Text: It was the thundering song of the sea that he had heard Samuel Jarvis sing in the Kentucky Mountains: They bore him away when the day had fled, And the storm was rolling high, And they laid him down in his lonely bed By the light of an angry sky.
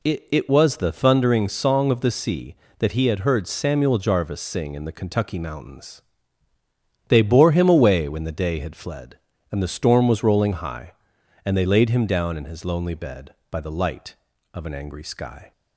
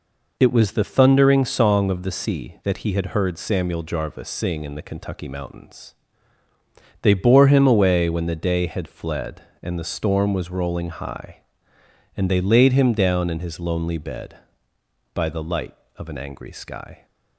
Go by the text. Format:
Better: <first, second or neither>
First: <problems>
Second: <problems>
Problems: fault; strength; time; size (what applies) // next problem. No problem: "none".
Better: second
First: says "It" twice; at 0.3 s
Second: none